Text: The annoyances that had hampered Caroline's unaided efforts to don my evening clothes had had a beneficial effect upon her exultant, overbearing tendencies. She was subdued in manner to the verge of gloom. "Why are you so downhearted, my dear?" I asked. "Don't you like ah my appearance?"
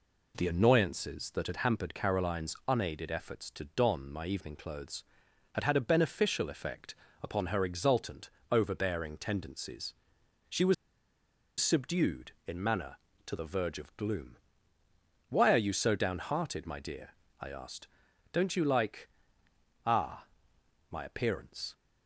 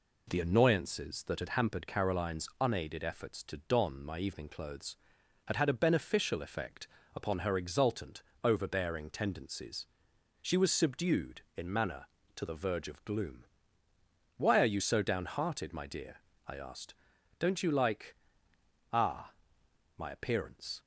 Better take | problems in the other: second | pauses between "effect" and "upon"; slight; at 6.9 s; 0.28 s long; slight in the second // pauses between "was" and "subdued"; noticeable; at 10.7 s; 0.86 s long // pauses between "like" and "ah"; noticeable; at 19.0 s; 0.76 s long; noticeable in the second // pauses between "ah" and "my"; noticeable; at 20.2 s; 0.64 s long; noticeable in the second

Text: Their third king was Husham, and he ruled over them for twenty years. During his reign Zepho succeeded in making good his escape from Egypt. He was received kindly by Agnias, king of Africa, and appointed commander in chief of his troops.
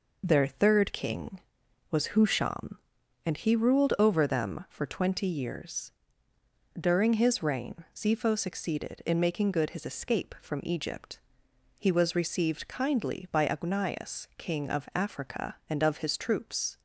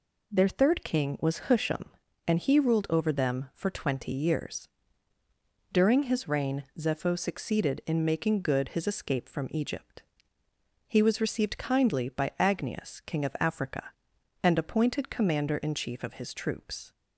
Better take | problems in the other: second | skips "appointed commander in chief"; at 15.8 s

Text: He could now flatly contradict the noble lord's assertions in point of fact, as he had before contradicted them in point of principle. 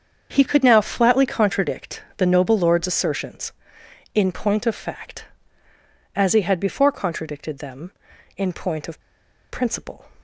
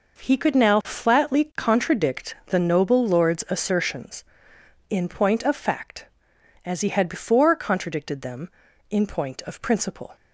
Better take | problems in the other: second | starts louder than the rest; strong; until 1.3 s; 7 dB // pauses between "of" and "principle"; noticeable; at 9.0 s; 0.49 s long

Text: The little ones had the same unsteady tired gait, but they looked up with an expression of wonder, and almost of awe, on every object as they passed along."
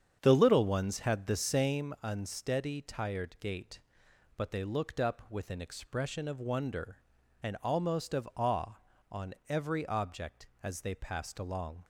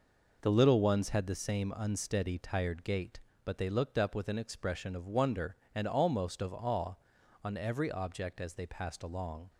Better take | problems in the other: second | starts louder than the rest; strong; until 1.8 s; 8 dB

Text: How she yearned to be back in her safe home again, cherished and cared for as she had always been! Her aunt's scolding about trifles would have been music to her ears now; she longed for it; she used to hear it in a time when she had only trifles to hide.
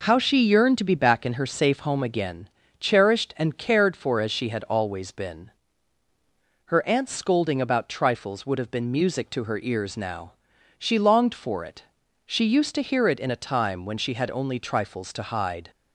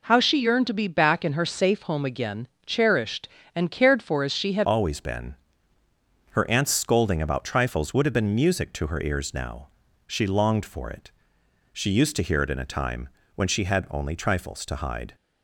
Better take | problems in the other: first | changes voice at "always"; from 4.6 s on; 10.5 s long // pauses between "time" and "when"; slight; at 13.0 s; 0.26 s long

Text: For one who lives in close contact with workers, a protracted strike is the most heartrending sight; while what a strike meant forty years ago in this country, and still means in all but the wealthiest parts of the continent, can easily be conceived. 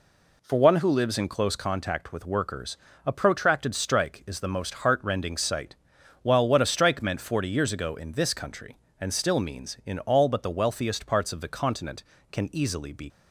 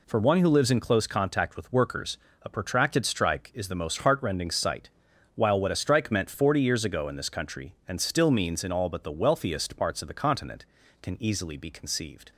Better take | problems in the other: second | stops before "conceived"; at 13.0 s

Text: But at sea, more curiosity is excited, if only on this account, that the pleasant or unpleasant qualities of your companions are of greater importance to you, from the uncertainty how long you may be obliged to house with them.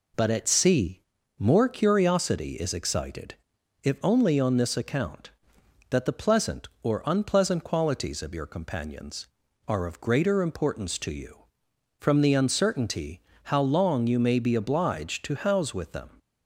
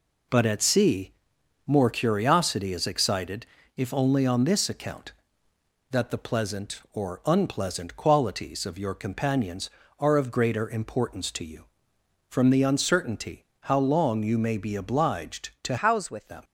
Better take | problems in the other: first | pauses between "uncertainty" and "how"; slight; at 13.4 s; 0.16 s long; slight in the first // changes voice from "house" to "with"; from 15.7 to 16.2 s; 0.5 s long

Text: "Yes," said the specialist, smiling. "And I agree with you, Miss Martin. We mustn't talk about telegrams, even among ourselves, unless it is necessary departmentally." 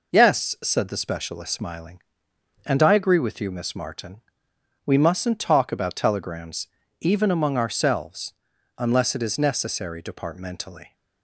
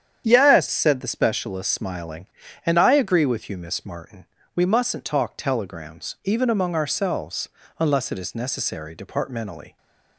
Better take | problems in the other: first | starts louder than the rest; strong; until 1.2 s; 8.5 dB // skips "about"; at 5.3 s

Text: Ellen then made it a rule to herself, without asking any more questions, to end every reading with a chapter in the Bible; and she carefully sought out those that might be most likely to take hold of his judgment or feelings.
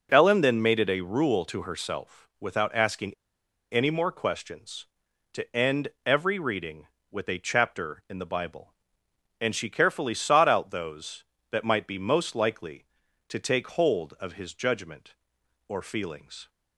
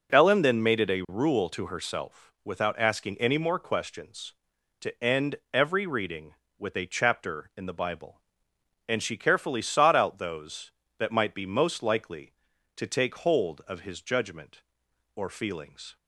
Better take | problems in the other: second | pauses between "asking" and "any"; noticeable; at 3.1 s; 0.57 s long // pauses between "end" and "every"; slight; at 5.8 s; 0.18 s long; slight in the second

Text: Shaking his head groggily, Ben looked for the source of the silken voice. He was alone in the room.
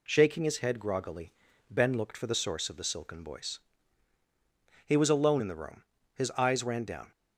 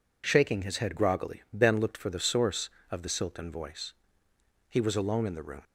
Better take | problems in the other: second | goes on to say "His eyes ran down"; noticeable; from 6.1 s on; 0.96 s long

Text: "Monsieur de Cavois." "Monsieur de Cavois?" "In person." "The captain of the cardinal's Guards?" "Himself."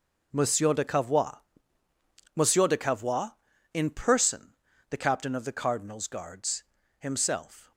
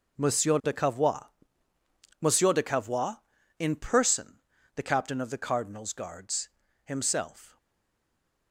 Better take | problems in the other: first | stays silent after the last word; from 7.5 s on; 1.0 s long

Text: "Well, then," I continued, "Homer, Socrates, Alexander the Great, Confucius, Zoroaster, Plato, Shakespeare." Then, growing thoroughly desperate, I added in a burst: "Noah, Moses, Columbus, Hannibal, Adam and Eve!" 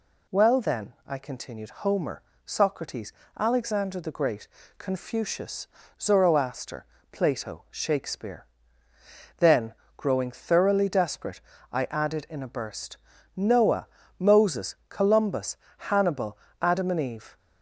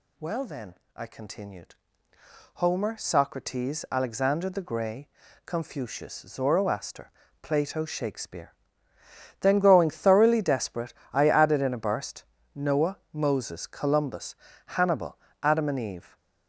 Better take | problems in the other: first | says "Grey" for "Great"; at 4.6 s

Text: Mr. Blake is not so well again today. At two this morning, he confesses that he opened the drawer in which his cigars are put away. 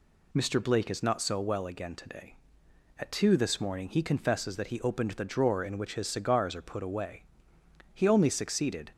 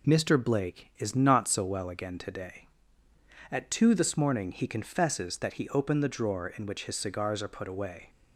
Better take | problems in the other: second | goes on to say "He only succeeded"; noticeable; from 7.9 s on; 0.98 s long

